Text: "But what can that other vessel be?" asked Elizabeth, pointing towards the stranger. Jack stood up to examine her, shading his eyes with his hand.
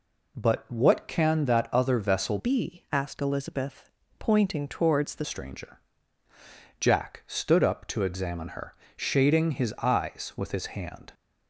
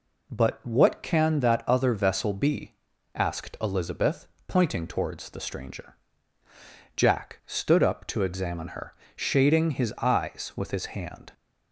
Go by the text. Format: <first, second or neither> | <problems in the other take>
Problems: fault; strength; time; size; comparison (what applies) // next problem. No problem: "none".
second | changes voice from "be" to "the"; from 2.3 to 5.2 s; 2.9 s long